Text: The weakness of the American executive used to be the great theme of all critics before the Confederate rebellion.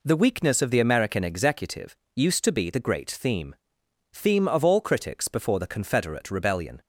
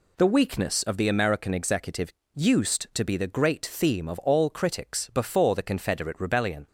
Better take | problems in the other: second | pauses between "executive" and "used"; slight; at 1.9 s; 0.22 s long; slight in the second // says "theme" twice; at 4.1 s

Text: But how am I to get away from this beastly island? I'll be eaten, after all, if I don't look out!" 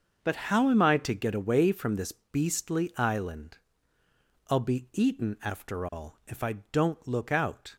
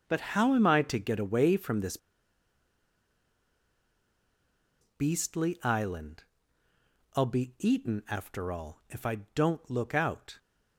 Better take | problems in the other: first | starts louder than the rest; until 1.0 s; 6 dB; also in the first // pauses between "this" and "beastly"; strong; at 1.9 s; 2.8 s long // pauses between "I" and "don't"; slight; at 9.1 s; 0.18 s long; slight in the first

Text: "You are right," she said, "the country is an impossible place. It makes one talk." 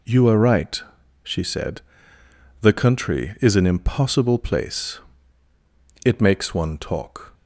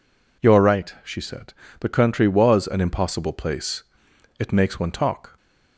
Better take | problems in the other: first | says "was" for "is"; at 2.2 s

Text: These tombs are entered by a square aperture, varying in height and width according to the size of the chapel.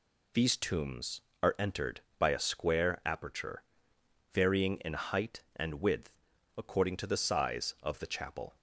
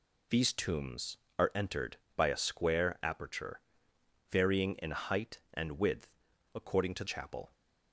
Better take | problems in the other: first | pauses between "width" and "according"; noticeable; at 6.0 s; 0.48 s long; noticeable in the first // skips "the size of the"; at 7.0 s

